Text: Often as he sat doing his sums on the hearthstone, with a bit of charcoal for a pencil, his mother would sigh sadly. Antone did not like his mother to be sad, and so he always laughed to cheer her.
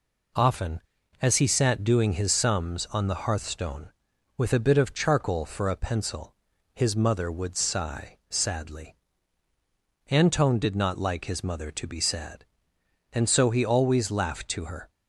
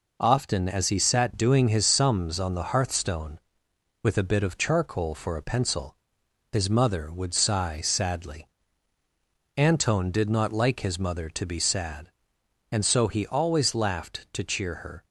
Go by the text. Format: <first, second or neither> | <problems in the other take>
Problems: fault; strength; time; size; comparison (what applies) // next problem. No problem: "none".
second | skips "cheer"; at 14.6 s